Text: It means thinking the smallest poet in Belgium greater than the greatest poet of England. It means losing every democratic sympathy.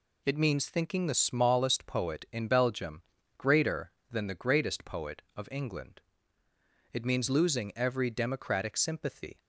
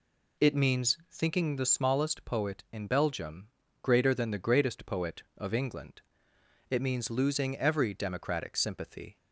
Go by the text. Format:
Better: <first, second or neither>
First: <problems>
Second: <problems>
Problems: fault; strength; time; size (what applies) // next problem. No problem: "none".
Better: neither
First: pauses between "Belgium" and "greater"; slight; at 3.0 s; 0.34 s long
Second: pauses between "Belgium" and "greater"; slight; at 3.4 s; 0.34 s long